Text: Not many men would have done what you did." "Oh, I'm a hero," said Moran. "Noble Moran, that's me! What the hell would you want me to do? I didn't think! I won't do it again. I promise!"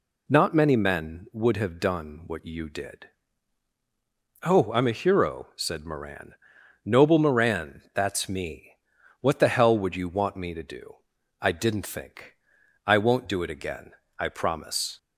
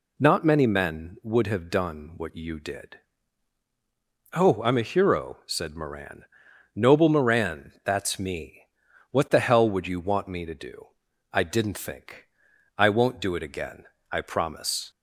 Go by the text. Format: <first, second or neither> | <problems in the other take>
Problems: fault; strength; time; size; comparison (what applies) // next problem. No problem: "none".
neither | none